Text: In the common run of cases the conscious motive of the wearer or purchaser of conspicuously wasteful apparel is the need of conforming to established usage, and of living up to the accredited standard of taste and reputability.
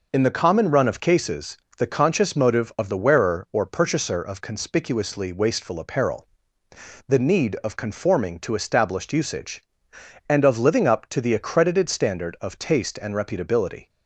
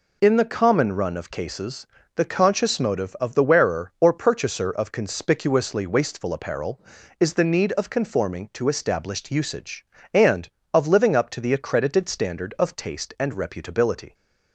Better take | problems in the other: second | pauses between "cases" and "the"; slight; at 1.5 s; 0.18 s long; slight in the second // skips "is"; at 6.6 s

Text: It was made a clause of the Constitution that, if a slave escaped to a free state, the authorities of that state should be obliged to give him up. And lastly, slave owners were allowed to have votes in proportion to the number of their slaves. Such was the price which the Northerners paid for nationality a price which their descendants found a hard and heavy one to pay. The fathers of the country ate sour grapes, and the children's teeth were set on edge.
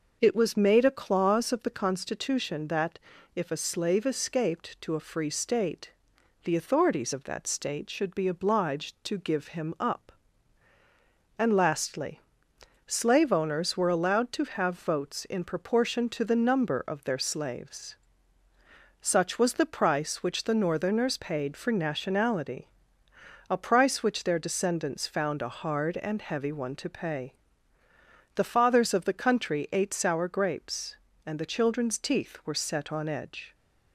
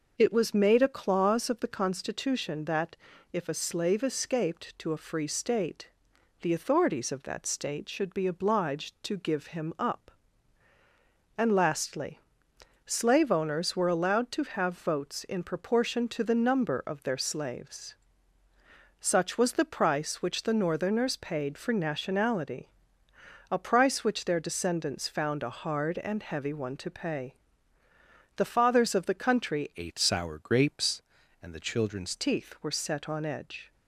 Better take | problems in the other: first | pauses between "nationality" and "a"; noticeable; at 22.6 s; 0.80 s long; noticeable in the first // changes voice from "ate" to "children's"; from 29.7 to 32.1 s; 2.4 s long

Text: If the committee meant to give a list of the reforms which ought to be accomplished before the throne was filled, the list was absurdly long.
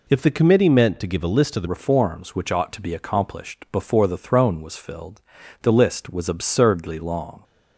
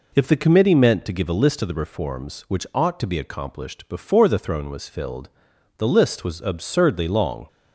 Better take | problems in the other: second | changes voice at "reforms"; from 1.6 s on; 5.8 s long

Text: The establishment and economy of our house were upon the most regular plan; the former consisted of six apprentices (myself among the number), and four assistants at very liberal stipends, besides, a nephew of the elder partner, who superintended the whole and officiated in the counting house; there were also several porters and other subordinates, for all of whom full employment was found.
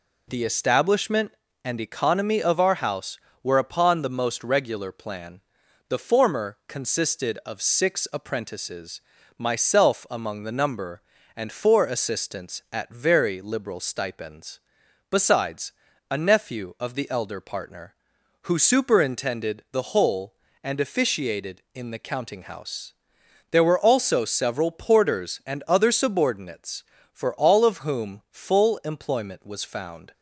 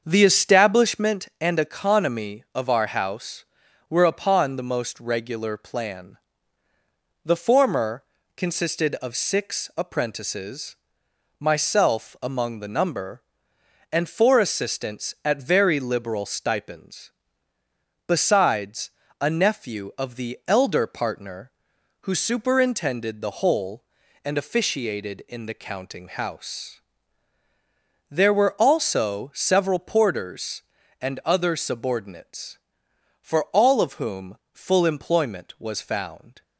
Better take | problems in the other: first | starts louder than the rest; until 1.2 s; 7 dB // pauses between "former" and "consisted"; slight; at 8.0 s; 0.32 s long // pauses between "whom" and "full"; slight; at 34.3 s; 0.16 s long

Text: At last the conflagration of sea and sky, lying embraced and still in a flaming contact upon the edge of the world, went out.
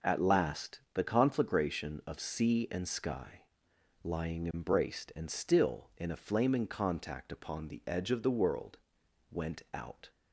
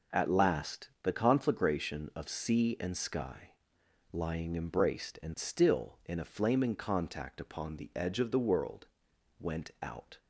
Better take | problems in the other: neither | none

